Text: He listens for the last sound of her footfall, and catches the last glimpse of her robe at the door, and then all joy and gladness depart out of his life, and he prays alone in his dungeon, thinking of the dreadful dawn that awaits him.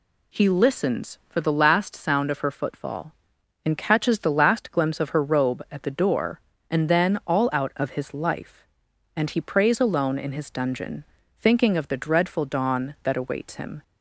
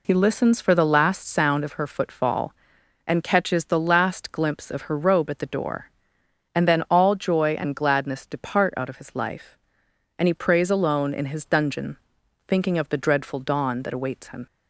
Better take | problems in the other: second | skips "joy and gladness depart"; at 7.5 s

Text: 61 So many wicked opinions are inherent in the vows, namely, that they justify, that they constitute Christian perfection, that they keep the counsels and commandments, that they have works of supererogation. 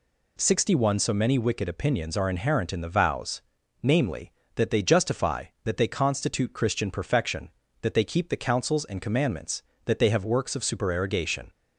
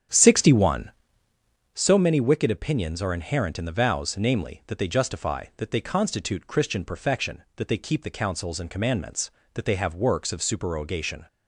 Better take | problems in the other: first | starts louder than the rest; strong; until 2.0 s; 9 dB

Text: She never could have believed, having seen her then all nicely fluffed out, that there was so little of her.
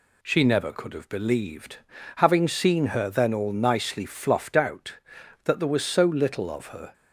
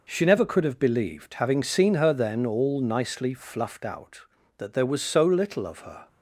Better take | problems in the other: neither | none

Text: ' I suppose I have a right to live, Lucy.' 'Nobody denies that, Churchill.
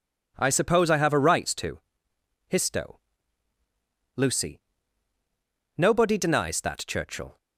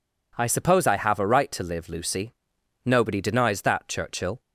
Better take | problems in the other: second | says "histo" for "live"; at 2.5 s

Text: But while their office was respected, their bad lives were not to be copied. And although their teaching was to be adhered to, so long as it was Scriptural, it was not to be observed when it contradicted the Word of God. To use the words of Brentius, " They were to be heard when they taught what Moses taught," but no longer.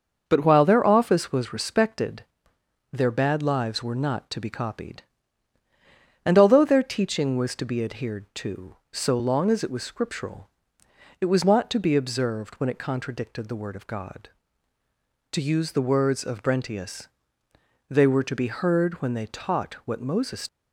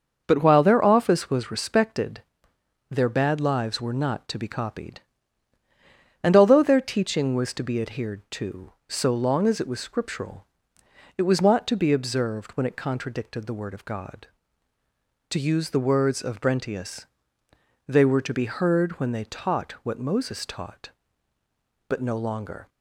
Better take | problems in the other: second | starts louder than the rest; until 1.2 s; 6.5 dB; also in the second // stops before "taught but no longer"; at 20.4 s

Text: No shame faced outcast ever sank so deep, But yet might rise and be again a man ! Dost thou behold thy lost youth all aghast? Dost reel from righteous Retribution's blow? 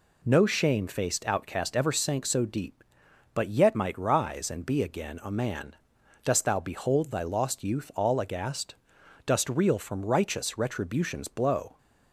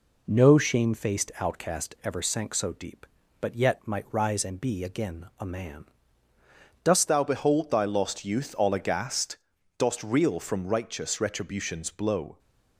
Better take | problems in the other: first | changes voice at "thou"; from 7.0 s on; 5.3 s long

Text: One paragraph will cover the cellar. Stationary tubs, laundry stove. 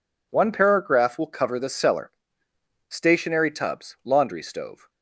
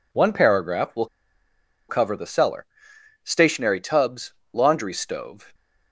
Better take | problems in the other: first | pauses between "will" and "cover"; noticeable; at 1.0 s; 0.83 s long

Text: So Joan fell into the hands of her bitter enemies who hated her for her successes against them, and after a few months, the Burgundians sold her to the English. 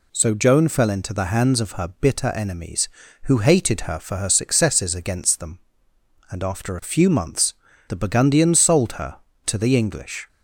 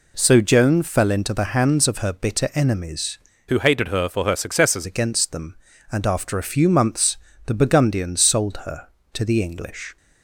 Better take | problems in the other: first | changes voice from "who" to "successes"; from 3.4 to 4.8 s; 1.4 s long

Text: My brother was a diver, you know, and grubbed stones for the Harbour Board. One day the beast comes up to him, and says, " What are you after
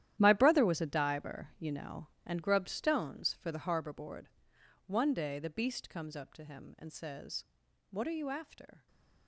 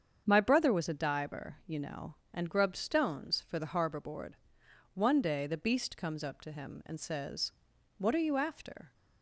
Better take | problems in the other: second | gets quieter; strong; throughout; 19 dB // starts louder than the rest; strong; until 1.1 s; 12 dB; strong in the second

